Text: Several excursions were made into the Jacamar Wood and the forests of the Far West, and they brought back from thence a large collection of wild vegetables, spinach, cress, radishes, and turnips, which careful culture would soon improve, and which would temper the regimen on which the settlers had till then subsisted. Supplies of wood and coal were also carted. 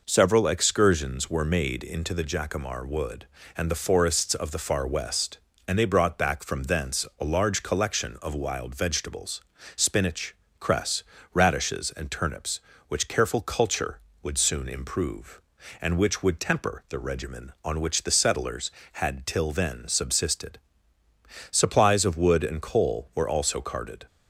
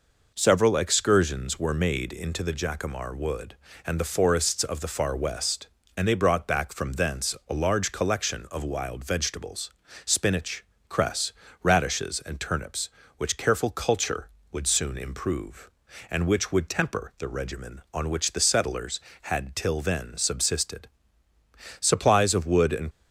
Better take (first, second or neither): first